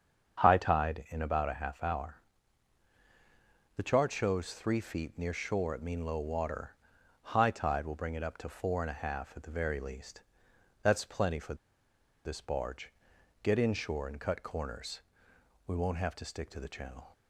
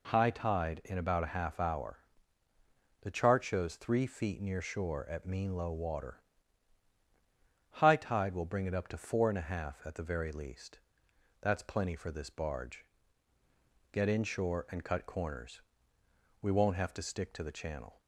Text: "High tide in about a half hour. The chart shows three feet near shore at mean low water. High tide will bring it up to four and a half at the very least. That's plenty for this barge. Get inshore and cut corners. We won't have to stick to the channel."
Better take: second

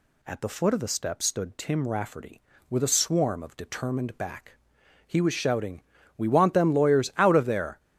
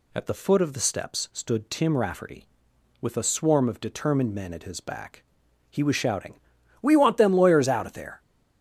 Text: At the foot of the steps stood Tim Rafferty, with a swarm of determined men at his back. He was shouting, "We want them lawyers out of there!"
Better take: second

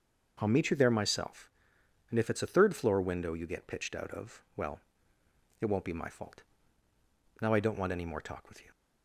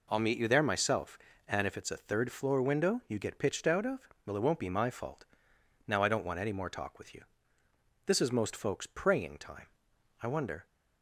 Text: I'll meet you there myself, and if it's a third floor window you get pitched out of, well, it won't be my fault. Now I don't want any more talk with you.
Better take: first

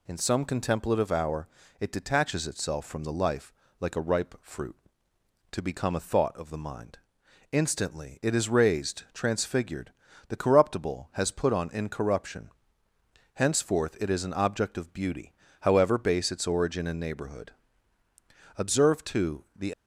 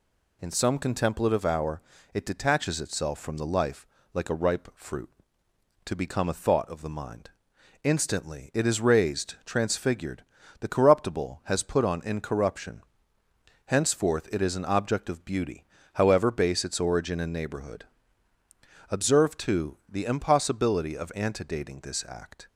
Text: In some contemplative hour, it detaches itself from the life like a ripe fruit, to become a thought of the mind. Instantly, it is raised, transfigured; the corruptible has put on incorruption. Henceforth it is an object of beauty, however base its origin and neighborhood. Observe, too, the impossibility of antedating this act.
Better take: second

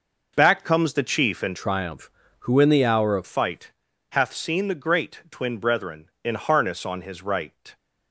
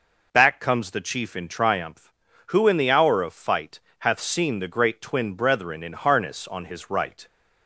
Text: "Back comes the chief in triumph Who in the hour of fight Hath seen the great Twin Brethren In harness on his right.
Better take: second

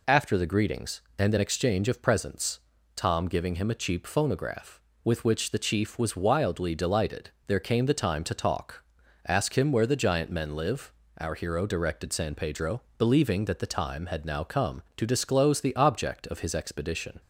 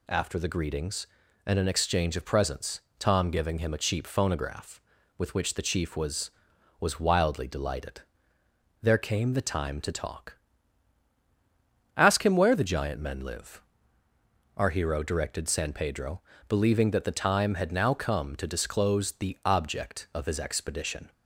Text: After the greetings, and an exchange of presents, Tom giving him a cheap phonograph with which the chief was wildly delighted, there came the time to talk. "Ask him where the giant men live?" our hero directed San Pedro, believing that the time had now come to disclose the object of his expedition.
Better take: first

